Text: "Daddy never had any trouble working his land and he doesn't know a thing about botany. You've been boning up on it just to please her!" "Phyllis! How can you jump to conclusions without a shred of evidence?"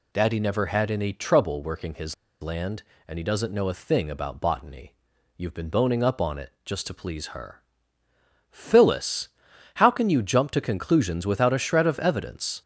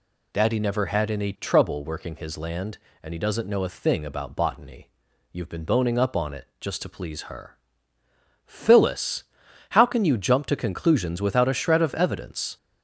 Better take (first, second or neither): second